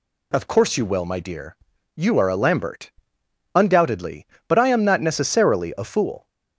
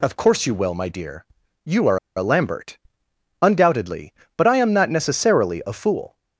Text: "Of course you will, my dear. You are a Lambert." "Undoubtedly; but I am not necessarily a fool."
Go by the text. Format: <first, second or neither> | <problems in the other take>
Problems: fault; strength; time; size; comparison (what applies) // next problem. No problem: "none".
first | pauses between "are" and "a"; slight; at 1.9 s; 0.18 s long